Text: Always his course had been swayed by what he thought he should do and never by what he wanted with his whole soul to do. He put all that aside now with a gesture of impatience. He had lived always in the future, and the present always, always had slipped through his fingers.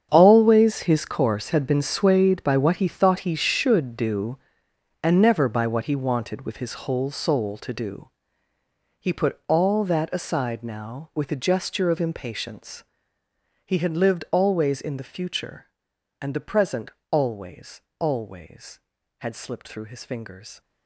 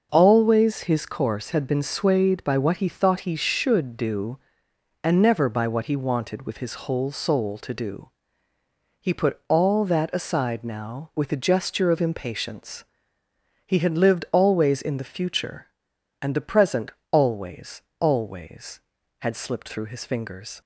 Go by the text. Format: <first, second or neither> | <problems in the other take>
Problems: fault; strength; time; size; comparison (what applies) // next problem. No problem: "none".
second | gets quieter; strong; throughout; 14.5 dB // starts louder than the rest; strong; until 1.1 s; 8 dB; also in the second // pauses between "present" and "always"; slight; at 16.8 s; 0.22 s long; slight in the second